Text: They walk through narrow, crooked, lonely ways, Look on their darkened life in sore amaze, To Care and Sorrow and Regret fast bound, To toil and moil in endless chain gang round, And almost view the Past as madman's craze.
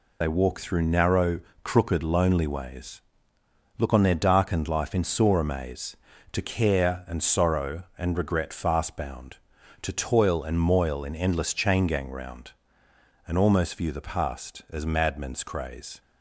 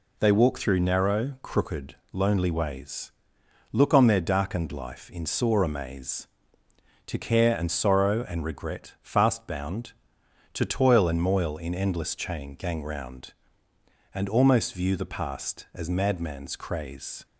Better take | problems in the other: second | loses the start of "They"; at 0.2 s; 45 ms

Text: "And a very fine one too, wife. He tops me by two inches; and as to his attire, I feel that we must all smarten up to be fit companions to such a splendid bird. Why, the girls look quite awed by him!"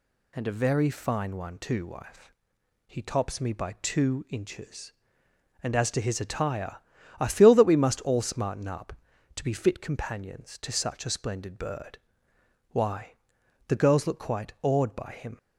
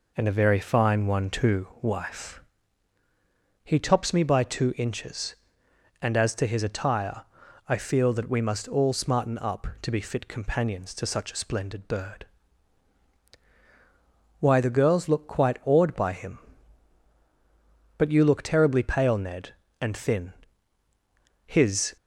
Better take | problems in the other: first | goes on to say "But you look terribly pale Ned and thin his"; strong; from 17.9 s on; 3.9 s long

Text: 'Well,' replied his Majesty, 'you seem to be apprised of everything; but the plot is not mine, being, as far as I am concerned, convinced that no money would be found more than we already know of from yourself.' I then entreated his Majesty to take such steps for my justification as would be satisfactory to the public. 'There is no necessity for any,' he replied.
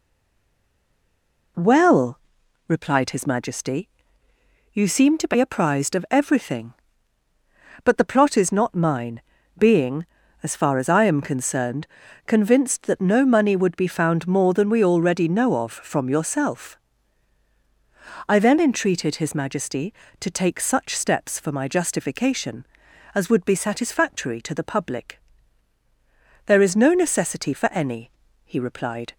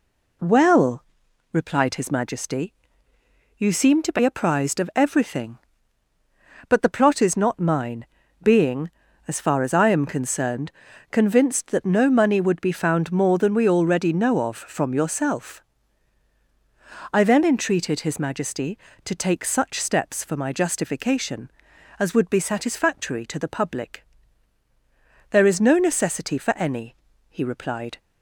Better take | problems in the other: second | stays silent before the first word; noticeable; until 1.5 s; 1.5 s long

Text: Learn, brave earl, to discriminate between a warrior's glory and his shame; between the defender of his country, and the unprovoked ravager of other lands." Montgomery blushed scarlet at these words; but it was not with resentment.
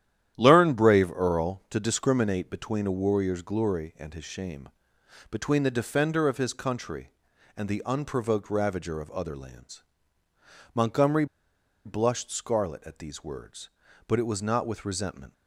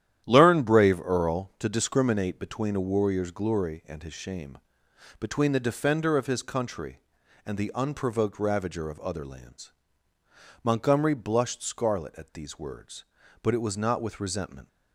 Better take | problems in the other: second | starts louder than the rest; strong; until 1.3 s; 11 dB; strong in the second // pauses between "Montgomery" and "blushed"; noticeable; at 11.2 s; 0.60 s long

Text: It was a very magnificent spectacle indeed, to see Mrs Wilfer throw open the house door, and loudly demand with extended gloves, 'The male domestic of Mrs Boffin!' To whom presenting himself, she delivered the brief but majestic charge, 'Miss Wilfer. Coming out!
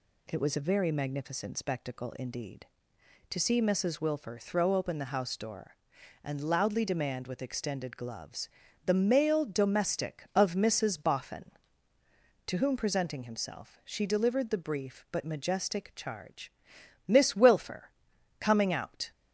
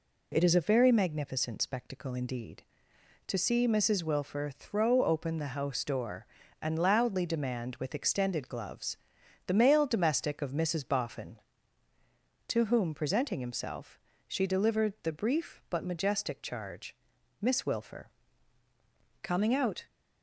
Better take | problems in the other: first | says "is" for "was"; at 0.4 s

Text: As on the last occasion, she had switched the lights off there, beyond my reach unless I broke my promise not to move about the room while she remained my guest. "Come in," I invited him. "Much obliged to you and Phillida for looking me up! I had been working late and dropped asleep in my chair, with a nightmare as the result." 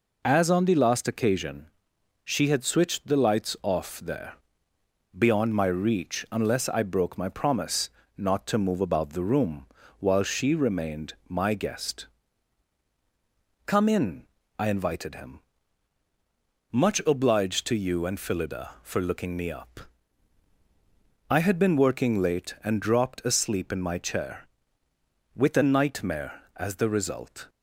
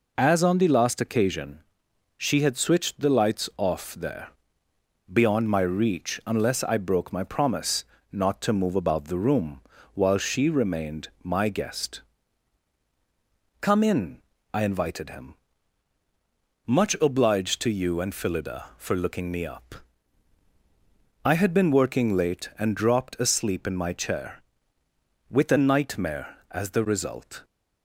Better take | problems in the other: neither | pauses between "promise" and "not"; slight; the same in both // pauses between "room" and "while"; slight; the same in both // pauses between "remained" and "my"; slight; the same in both

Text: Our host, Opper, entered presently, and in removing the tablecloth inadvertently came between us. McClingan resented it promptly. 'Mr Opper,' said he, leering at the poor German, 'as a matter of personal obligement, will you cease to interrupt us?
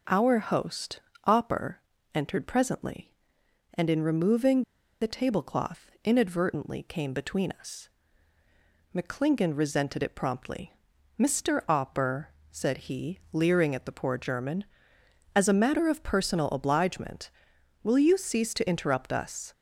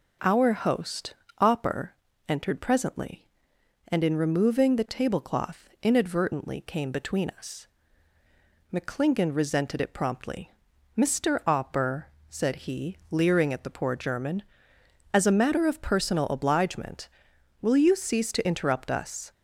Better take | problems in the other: second | pauses between "removing" and "the"; at 4.6 s; 0.38 s long

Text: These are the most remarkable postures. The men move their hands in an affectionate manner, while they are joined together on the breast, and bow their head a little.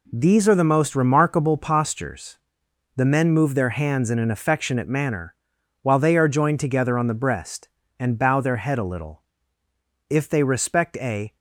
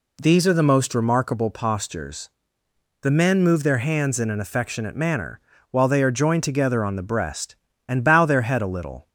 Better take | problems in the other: second | goes on to say "If they respect a"; noticeable; from 10.0 s on; 1.2 s long

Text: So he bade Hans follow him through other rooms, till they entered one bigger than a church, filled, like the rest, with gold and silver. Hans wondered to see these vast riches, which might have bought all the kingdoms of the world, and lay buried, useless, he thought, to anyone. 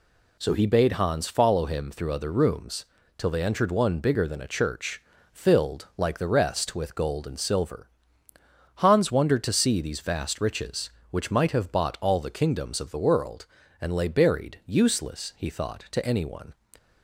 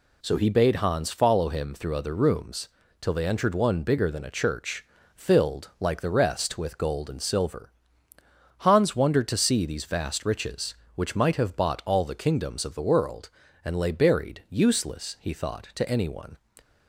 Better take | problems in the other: neither | none

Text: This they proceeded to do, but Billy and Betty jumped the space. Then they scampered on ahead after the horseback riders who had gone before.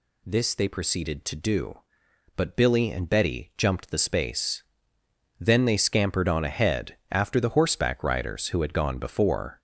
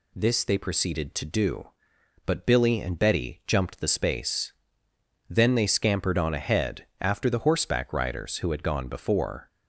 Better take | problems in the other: second | gets louder; noticeable; throughout; 4.5 dB // pauses between "ahead" and "after"; slight; at 6.9 s; 0.16 s long; slight in the second

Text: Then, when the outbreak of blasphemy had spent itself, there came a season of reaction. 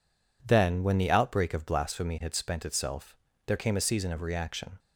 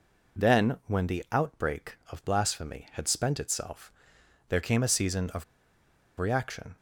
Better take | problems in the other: first | pauses between "of" and "reaction"; noticeable; at 5.4 s; 0.76 s long

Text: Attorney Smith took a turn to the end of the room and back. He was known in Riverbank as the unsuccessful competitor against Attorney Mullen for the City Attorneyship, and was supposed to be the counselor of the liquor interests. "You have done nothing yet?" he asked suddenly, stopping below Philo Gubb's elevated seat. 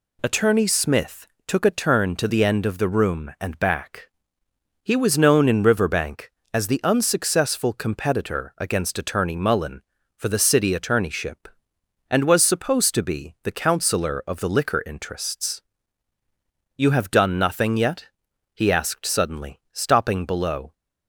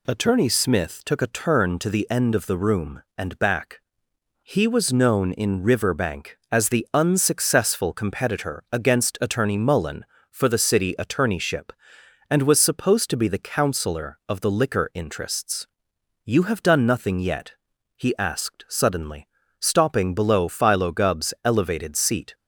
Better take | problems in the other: second | pauses between "Smith" and "took"; slight; at 1.2 s; 0.20 s long // stops before "Philo Gubb's elevated seat"; at 20.7 s

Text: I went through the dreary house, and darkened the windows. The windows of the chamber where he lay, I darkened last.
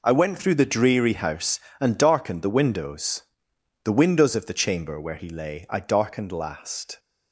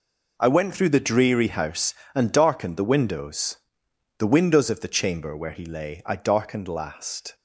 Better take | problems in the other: neither | none

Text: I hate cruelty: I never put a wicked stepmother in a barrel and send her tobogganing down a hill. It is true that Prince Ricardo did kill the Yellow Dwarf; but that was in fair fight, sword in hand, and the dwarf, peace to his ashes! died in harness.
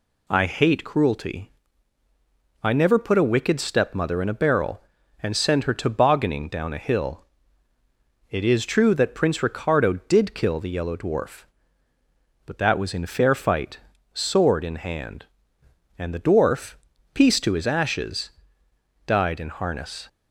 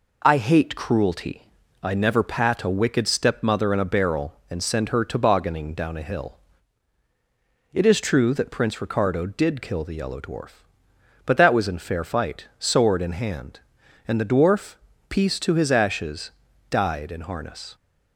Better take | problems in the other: first | says "pat" for "put"; at 2.2 s

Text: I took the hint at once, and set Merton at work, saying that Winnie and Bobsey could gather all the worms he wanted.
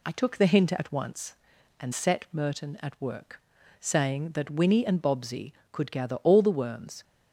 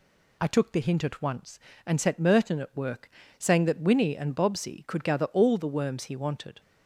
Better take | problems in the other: second | stops before "he wanted"; at 7.0 s

